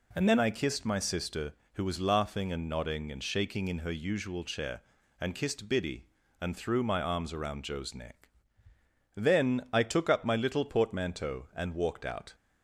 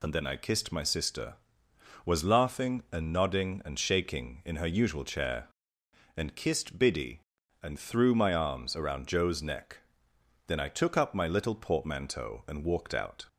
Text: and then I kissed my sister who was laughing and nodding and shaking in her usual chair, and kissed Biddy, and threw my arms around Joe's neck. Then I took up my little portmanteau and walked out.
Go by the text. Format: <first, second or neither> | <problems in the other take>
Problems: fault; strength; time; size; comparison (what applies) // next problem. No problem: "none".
first | skips "who"; at 1.6 s